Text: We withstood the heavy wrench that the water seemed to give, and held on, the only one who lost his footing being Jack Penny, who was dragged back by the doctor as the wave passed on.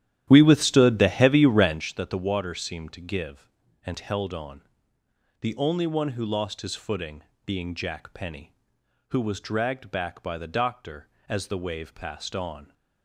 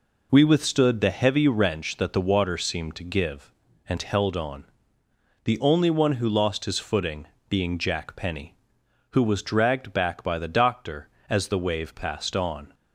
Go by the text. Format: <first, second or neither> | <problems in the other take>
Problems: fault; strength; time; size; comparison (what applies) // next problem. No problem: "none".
second | starts louder than the rest; strong; until 1.9 s; 12 dB // pauses between "footing" and "being"; slight; at 7.2 s; 0.22 s long; slight in the second